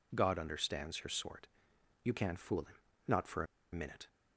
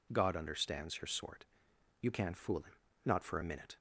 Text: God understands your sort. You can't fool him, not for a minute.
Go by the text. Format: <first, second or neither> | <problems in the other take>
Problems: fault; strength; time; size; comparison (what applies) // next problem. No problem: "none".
second | pauses between "a" and "minute"; slight; at 3.4 s; 0.27 s long